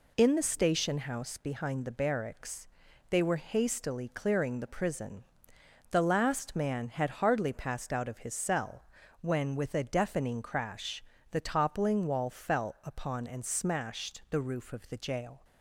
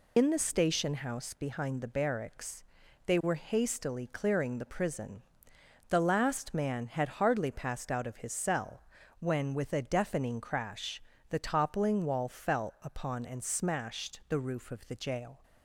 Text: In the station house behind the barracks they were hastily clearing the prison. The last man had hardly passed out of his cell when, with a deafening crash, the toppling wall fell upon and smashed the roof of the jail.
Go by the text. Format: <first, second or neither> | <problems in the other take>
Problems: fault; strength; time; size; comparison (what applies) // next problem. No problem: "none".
first | loses the start of "In"; at 0.1 s; 60 ms // pauses between "barracks" and "they"; at 2.6 s; 0.40 s long; also in the first // pauses between "cell" and "when"; at 8.8 s; 0.40 s long; also in the first